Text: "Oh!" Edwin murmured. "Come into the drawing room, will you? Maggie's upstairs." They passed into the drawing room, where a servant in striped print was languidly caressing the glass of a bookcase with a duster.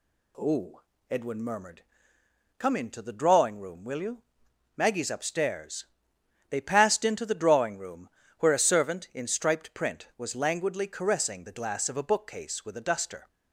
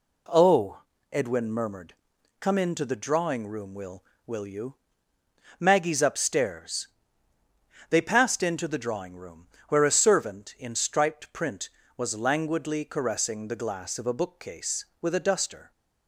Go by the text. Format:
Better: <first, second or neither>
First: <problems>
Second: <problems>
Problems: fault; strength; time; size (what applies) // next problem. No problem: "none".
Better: first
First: none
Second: says "will" twice; at 4.2 s